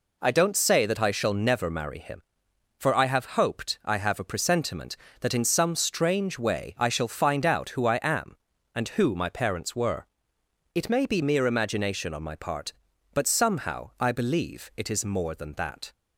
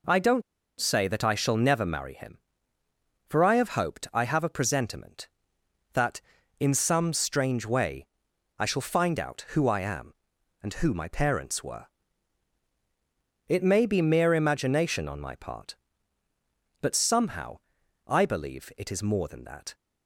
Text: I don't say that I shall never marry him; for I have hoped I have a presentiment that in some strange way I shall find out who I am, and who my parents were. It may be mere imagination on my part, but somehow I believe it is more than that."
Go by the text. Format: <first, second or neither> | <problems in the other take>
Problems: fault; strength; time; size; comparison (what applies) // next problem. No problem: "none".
first | pauses between "don't" and "say"; at 0.4 s; 0.38 s long // pauses between "way" and "I"; noticeable; at 8.0 s; 0.52 s long // pauses between "somehow" and "I"; noticeable; at 17.5 s; 0.48 s long